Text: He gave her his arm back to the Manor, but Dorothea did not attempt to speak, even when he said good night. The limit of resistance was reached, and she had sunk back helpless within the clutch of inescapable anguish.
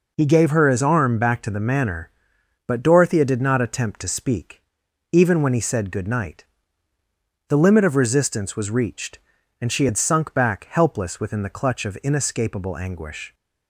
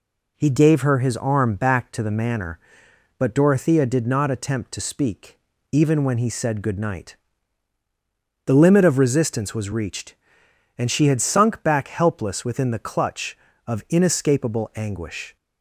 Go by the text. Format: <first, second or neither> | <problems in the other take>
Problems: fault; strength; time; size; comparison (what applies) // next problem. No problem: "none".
neither | none